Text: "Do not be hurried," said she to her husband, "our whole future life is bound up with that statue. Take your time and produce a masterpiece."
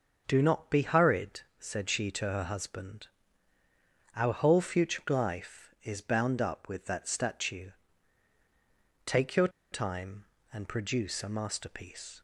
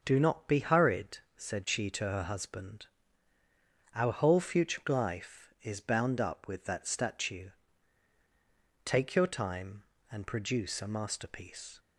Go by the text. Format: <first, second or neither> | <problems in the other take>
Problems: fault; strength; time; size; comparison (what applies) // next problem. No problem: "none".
second | starts louder than the rest; until 1.2 s; 6.5 dB; also in the second // pauses between "your" and "time"; slight; at 9.4 s; 0.23 s long